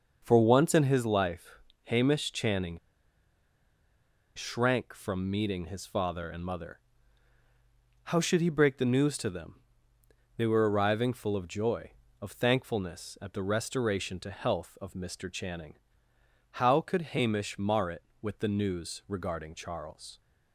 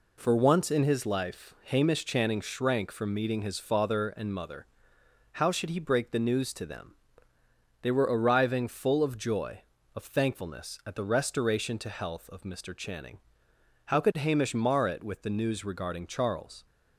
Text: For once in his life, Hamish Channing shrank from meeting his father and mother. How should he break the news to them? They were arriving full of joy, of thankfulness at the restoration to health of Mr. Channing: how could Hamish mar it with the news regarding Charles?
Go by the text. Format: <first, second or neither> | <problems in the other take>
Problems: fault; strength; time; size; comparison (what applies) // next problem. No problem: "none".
second | starts louder than the rest; until 1.2 s; 6.5 dB // pauses between "Channing" and "shrank"; strong; at 2.7 s; 1.5 s long